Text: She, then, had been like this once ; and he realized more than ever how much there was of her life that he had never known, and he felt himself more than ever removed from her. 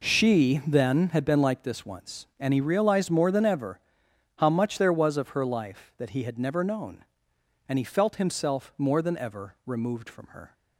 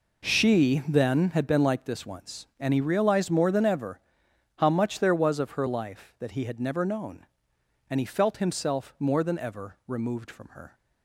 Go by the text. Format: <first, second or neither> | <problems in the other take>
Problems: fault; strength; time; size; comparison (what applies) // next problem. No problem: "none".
neither | pauses between "ever" and "how"; noticeable; the same in both